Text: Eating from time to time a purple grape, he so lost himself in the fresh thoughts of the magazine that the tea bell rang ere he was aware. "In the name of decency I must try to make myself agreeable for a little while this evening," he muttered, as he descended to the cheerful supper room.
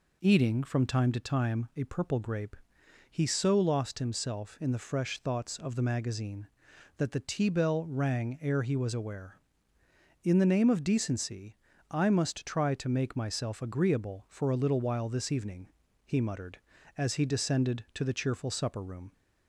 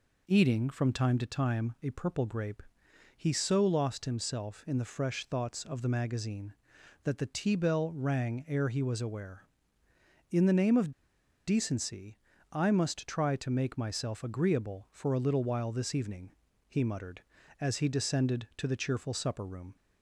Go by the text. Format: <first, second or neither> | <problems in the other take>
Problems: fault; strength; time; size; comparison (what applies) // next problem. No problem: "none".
first | pauses between "of" and "decency"; noticeable; at 10.9 s; 0.55 s long // pauses between "decency" and "I"; slight; at 12.1 s; 0.34 s long; slight in the first